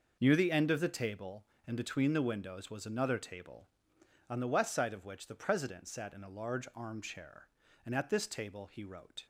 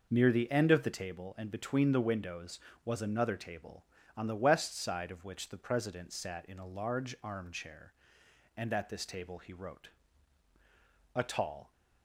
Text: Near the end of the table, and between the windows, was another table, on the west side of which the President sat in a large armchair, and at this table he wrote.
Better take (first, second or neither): first